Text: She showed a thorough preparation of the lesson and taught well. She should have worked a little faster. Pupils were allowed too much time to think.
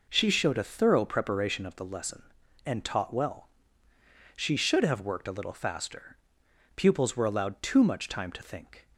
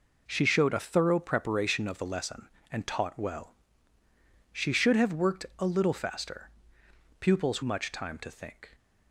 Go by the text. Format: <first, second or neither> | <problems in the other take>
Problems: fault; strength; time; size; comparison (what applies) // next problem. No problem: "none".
first | skips "were allowed too"; at 7.6 s